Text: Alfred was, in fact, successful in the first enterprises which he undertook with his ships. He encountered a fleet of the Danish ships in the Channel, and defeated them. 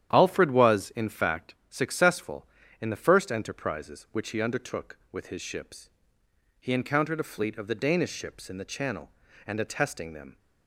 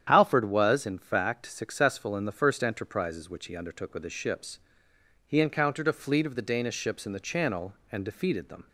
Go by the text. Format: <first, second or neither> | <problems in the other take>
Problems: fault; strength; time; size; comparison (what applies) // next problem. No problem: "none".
second | starts louder than the rest; strong; until 1.1 s; 10 dB; strong in the second // says "attesting" for "defeated"; at 9.6 s